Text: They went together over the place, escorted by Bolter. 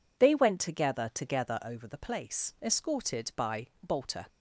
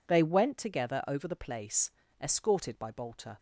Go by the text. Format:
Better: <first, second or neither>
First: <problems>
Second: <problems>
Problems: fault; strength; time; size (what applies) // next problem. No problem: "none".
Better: second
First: says "together" twice; at 1.1 s // pauses between "by" and "Bolter"; slight; at 3.6 s; 0.16 s long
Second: none